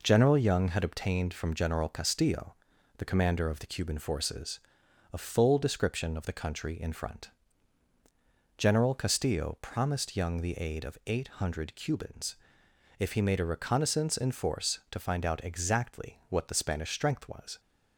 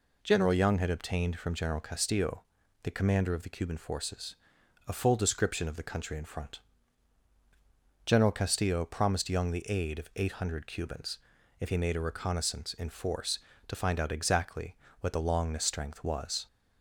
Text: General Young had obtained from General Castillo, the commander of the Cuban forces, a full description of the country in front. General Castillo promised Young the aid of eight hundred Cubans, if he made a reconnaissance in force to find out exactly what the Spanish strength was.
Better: first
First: none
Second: pauses between "exactly" and "what"; slight; at 14.7 s; 0.26 s long // says "Longness" for "Spanish"; at 15.2 s

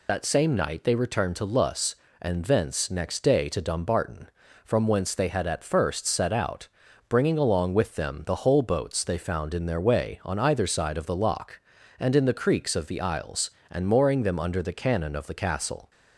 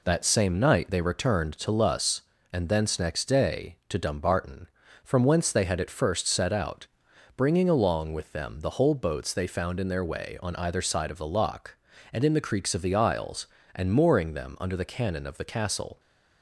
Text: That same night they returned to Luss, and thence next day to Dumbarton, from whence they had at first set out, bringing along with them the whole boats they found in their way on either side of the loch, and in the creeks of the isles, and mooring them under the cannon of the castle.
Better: second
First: loses the start of "That"; at 0.0 s; 35 ms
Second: none

